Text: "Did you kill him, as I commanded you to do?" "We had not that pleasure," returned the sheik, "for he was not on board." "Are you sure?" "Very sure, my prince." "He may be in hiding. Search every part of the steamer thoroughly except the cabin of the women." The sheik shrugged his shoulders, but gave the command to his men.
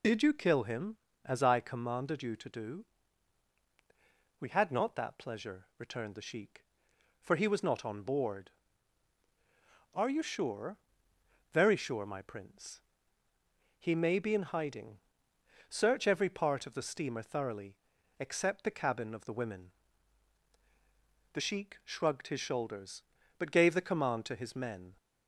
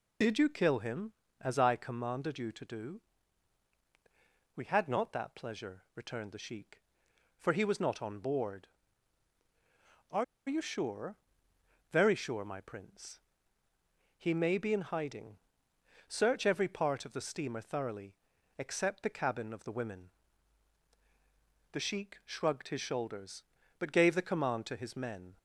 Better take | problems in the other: first | pauses between "Are" and "you"; slight; at 10.2 s; 0.24 s long // pauses between "thoroughly" and "except"; at 18.1 s; 0.44 s long; also in the first

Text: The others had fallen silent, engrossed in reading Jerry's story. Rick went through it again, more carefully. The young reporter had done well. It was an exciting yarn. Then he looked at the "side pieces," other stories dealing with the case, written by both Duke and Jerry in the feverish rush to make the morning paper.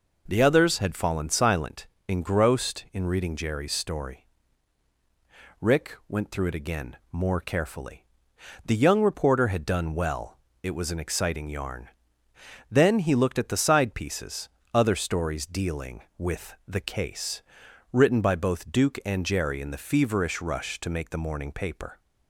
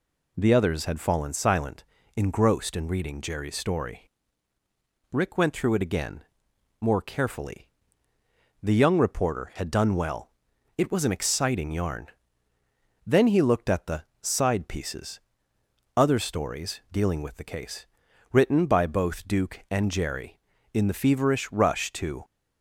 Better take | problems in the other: first | pauses between "the" and "side"; slight; at 14.0 s; 0.18 s long // stops before "make the morning paper"; at 22.2 s

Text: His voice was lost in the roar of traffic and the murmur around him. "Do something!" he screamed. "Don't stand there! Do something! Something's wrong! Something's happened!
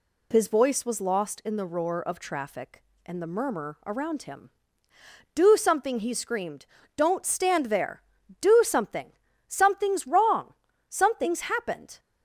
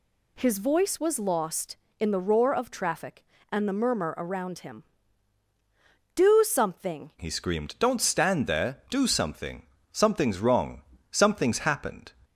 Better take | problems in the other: first | changes voice at "he"; from 7.2 s on; 4.9 s long

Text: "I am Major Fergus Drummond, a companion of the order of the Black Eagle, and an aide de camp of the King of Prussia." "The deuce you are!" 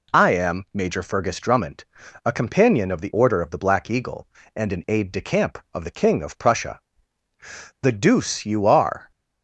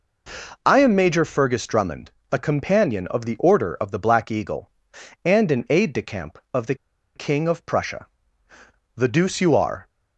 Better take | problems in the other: first | pauses between "the" and "King"; at 6.7 s; 0.40 s long

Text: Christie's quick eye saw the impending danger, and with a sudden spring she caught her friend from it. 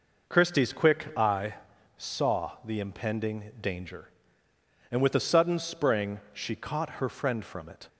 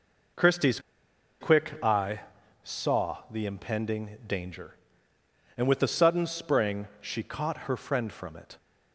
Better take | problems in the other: first | pauses between "Christie's" and "quick"; noticeable; at 0.7 s; 0.61 s long // pauses between "eye" and "saw"; at 2.2 s; 0.42 s long; also in the first

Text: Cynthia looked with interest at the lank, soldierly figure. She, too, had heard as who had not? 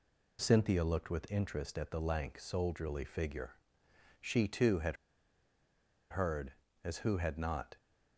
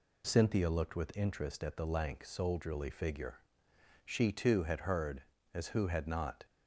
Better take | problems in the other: second | pauses between "had" and "heard"; at 4.9 s; 1.1 s long

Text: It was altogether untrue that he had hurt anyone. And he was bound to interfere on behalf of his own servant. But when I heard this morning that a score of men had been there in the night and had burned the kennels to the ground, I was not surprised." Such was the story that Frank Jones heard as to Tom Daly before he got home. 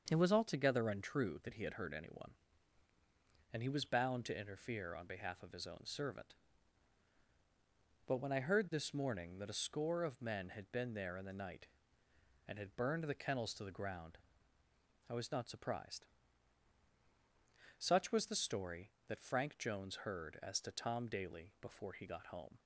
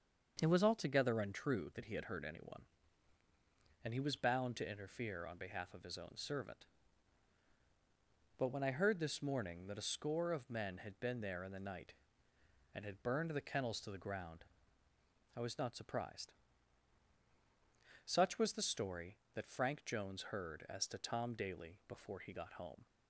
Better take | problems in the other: neither | starts louder than the rest; the same in both

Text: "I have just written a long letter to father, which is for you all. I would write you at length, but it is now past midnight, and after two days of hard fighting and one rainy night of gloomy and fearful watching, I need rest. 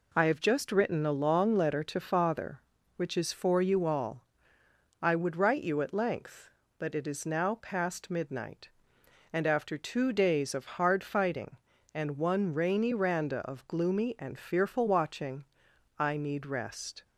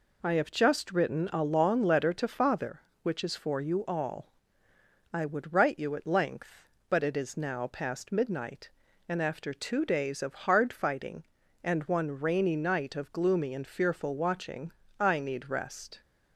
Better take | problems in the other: second | says "randa" for "night"; at 12.9 s

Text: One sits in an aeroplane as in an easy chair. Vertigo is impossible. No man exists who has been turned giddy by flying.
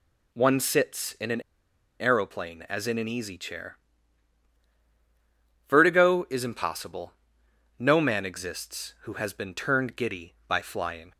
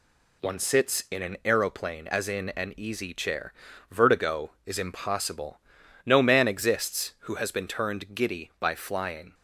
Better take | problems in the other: second | pauses between "an" and "aeroplane"; noticeable; at 1.3 s; 0.60 s long

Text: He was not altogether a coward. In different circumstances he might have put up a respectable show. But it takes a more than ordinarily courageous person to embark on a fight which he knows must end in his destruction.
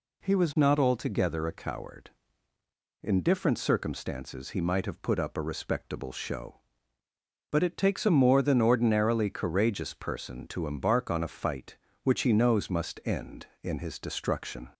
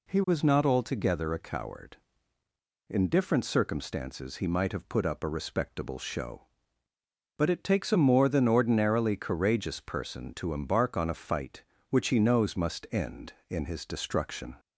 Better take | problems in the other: neither | none

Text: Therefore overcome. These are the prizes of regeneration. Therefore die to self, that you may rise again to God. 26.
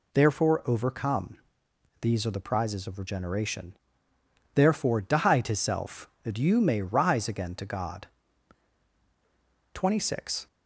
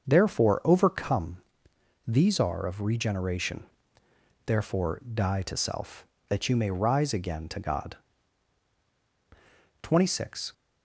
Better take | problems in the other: first | starts louder than the rest; until 1.1 s; 6.5 dB // skips "the prizes"; at 2.6 s

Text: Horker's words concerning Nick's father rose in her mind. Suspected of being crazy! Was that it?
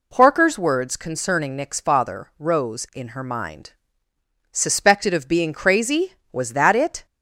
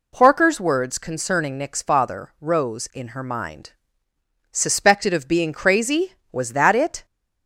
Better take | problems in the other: neither | none

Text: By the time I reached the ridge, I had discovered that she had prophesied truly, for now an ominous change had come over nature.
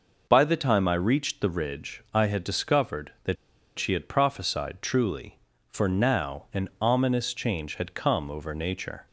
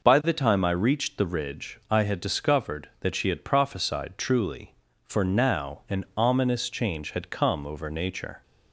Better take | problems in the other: second | pauses between "that" and "she"; at 3.3 s; 0.42 s long

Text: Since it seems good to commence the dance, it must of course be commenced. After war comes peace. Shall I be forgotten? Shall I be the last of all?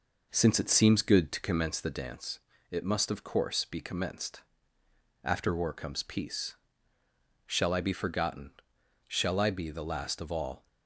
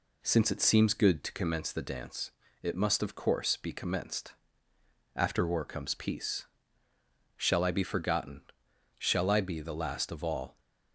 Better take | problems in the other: second | starts louder than the rest; noticeable; until 2.1 s; 5 dB

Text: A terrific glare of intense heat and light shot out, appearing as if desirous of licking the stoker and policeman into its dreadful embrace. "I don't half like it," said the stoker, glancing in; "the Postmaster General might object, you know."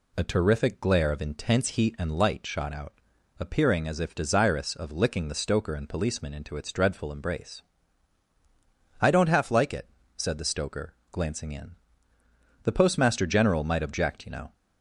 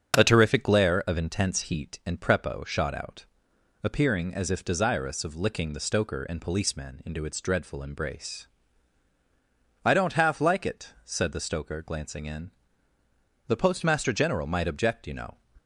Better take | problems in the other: first | starts louder than the rest; strong; until 1.2 s; 7 dB // says "prepo" for "light"; at 2.2 s

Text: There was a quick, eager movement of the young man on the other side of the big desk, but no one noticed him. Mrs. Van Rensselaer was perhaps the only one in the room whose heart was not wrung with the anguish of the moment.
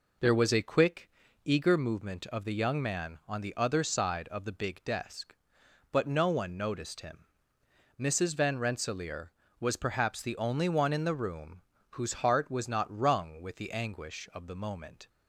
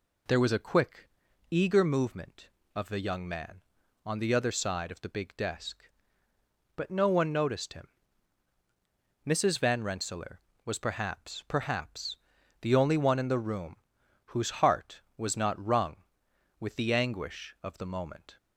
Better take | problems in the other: first | says "perhaps" twice; at 11.4 s // pauses between "room" and "whose"; noticeable; at 13.7 s; 0.50 s long; slight in the first

